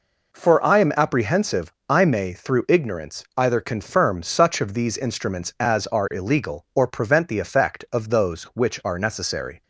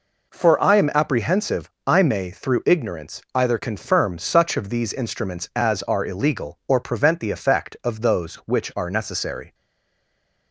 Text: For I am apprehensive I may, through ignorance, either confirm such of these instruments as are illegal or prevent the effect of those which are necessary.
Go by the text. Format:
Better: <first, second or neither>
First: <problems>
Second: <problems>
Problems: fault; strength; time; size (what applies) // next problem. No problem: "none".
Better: first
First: pauses between "apprehensive" and "I"; slight; at 1.7 s; 0.16 s long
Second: pauses between "apprehensive" and "I"; slight; at 1.7 s; 0.16 s long // stays silent after the last word; from 9.5 s on; 1.0 s long